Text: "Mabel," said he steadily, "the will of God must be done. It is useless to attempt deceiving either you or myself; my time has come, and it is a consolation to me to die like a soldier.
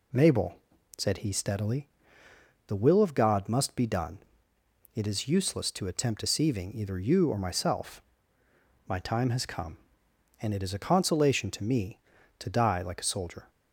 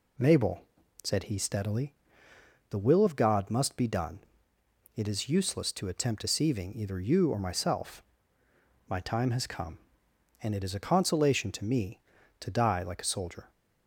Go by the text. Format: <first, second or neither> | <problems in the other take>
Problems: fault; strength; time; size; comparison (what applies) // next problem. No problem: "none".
neither | none